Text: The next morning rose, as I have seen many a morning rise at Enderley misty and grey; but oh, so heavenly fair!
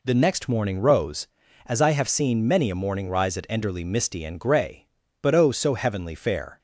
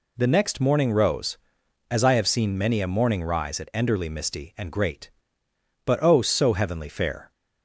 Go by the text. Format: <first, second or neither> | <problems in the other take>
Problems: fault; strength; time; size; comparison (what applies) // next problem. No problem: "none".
first | says "great" for "grey"; at 4.7 s